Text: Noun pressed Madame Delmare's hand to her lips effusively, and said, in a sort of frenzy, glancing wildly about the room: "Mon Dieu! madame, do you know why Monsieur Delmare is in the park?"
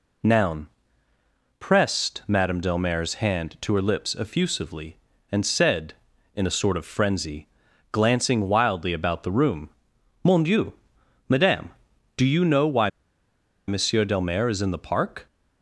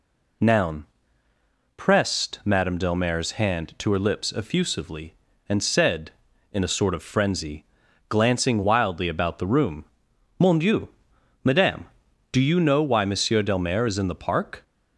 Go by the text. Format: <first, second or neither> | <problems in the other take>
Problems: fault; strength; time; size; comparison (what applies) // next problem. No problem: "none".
second | pauses between "Noun" and "pressed"; noticeable; at 0.6 s; 0.90 s long; noticeable in the second // pauses between "why" and "Monsieur"; noticeable; at 12.8 s; 0.79 s long